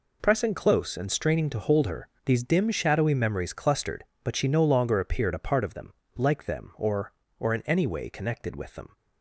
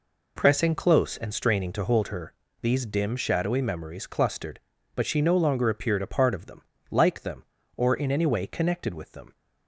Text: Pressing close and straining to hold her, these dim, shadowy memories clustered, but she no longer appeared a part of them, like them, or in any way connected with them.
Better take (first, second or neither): second